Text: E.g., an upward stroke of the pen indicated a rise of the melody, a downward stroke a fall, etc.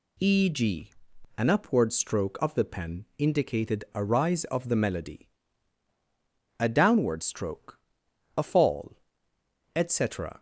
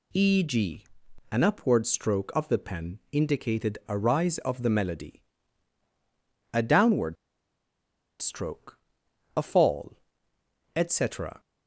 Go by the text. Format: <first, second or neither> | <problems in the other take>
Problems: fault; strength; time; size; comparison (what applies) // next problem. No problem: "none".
first | pauses between "downward" and "stroke"; at 7.1 s; 1.0 s long // pauses between "stroke" and "a"; noticeable; at 8.7 s; 0.58 s long; noticeable in the first